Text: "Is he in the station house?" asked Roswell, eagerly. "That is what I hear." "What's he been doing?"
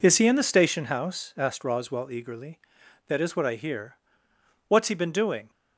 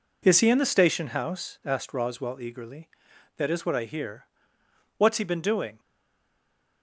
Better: first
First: none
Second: stays silent after the last word; from 5.7 s on; 1.1 s long

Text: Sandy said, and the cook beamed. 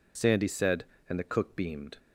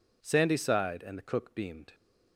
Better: first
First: none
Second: says "sighed" for "said"; at 0.5 s

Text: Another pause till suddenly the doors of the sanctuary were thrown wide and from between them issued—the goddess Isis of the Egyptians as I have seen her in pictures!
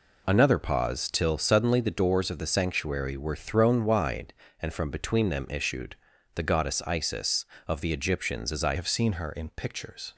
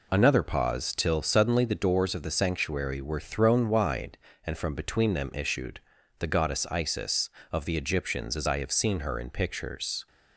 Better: second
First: changes voice at "have"; from 8.7 s on; 1.4 s long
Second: none

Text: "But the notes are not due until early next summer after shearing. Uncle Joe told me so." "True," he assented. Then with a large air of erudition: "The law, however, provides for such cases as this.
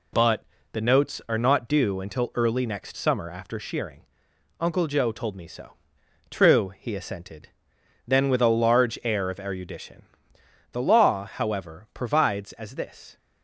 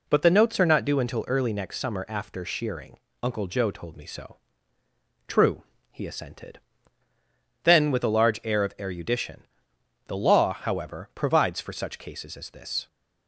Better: second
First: pauses between "But" and "the"; slight; at 0.4 s; 0.28 s long // skips "for such cases"; at 12.5 s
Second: none

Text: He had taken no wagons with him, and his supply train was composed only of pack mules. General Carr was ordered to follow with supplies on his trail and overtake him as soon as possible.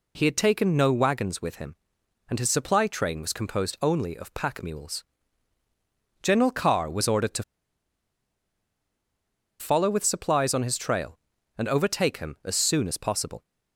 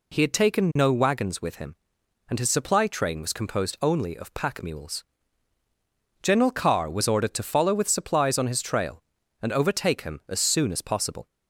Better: second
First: pauses between "to" and "follow"; strong; at 7.4 s; 2.1 s long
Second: none

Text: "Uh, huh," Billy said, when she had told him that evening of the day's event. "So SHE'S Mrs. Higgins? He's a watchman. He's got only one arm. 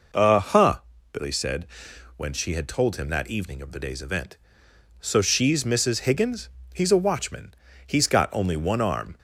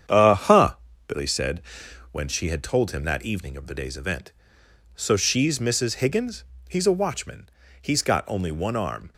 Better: first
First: none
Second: gets quieter; throughout; 6.5 dB

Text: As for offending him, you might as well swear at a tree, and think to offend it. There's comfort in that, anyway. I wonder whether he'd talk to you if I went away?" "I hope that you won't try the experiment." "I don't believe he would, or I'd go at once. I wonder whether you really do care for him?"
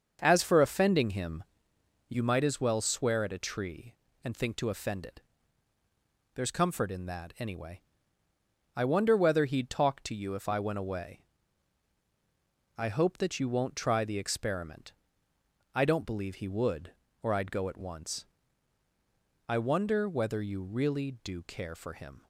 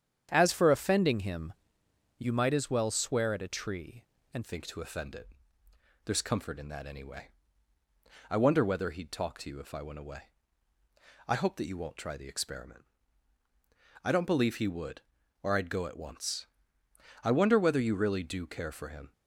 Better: first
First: starts louder than the rest; until 1.2 s; 6.5 dB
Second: starts louder than the rest; strong; until 1.3 s; 8.5 dB // changes voice at "think"; from 4.4 s on; 14.7 s long

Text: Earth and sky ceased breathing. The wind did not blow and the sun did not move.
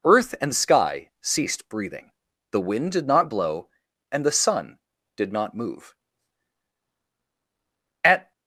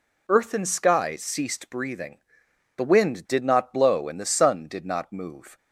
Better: second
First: goes on to say "At"; slight; from 8.0 s on; 0.28 s long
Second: none

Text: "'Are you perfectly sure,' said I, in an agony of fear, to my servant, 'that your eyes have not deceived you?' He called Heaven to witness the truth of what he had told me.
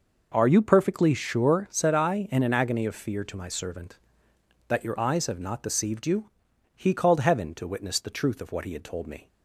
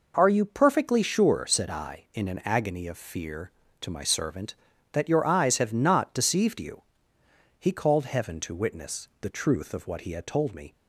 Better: neither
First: none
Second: none

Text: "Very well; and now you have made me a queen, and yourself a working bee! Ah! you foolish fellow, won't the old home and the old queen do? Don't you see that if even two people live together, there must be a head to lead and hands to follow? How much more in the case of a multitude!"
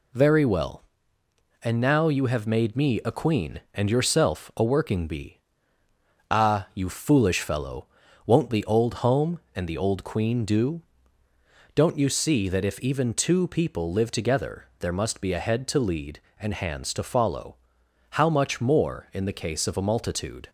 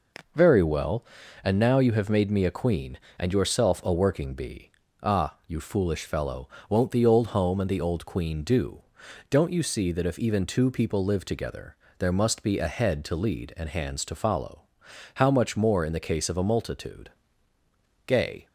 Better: first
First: none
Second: goes on to say "Gay"; slight; from 18.0 s on; 0.44 s long

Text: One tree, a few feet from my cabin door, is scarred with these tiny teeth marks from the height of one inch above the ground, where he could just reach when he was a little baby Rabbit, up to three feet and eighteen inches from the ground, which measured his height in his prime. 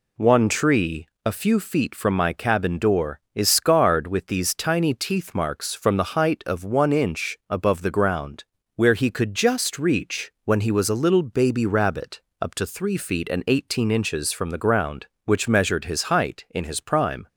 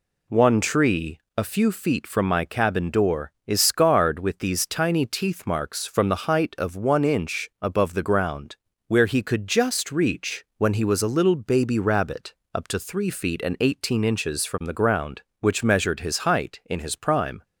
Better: neither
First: none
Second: none

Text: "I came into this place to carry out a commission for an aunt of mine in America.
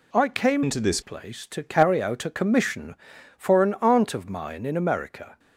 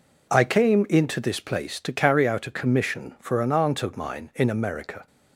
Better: second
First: changes voice from "into" to "this"; from 0.6 to 0.9 s; 0.3 s long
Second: none

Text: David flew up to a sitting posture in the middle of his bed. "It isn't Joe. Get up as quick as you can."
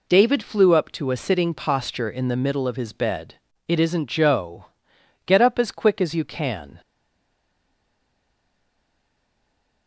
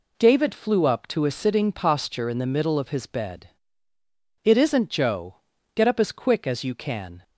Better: second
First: stays silent after the last word; strong; from 6.8 s on; 3.0 s long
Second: none

